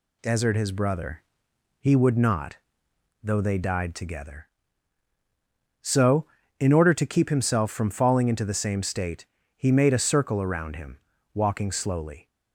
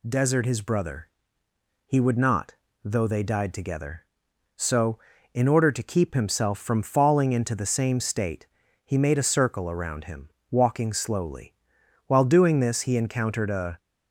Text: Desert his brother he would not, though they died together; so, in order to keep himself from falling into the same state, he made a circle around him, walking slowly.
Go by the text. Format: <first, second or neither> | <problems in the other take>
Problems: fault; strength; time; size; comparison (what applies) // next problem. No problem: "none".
first | pauses between "brother" and "he"; noticeable; at 1.0 s; 0.78 s long; noticeable in the first // goes on to say "While doing this he encountered a"; strong; from 12.0 s on; 1.7 s long